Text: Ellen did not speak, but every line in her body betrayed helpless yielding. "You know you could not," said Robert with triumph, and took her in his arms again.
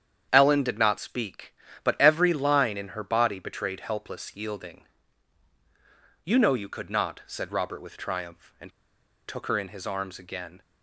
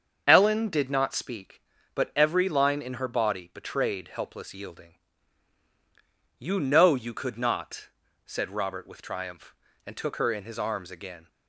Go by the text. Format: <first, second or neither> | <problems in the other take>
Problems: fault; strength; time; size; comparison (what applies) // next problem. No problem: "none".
second | starts louder than the rest; strong; until 1.3 s; 8.5 dB; also in the second // pauses between "and" and "took"; noticeable; at 8.7 s; 0.55 s long